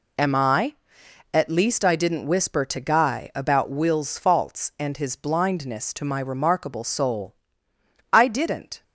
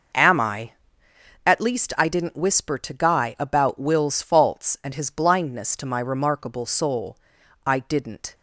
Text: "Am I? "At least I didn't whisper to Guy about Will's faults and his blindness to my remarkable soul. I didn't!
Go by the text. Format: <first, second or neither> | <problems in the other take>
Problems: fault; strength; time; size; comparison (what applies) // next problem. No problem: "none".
first | starts louder than the rest; noticeable; until 1.2 s; 5.5 dB